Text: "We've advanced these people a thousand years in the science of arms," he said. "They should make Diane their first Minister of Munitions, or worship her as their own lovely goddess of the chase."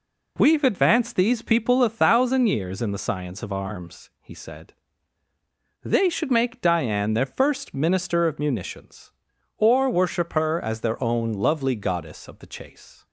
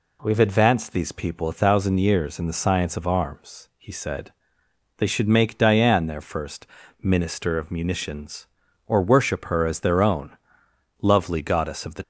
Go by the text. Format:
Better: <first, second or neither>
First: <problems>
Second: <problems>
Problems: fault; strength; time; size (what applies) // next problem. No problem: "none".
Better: first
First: none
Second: pauses between "first" and "Minister"; slight; at 6.6 s; 0.34 s long // pauses between "own" and "lovely"; noticeable; at 10.3 s; 0.64 s long // stops before "chase"; at 12.0 s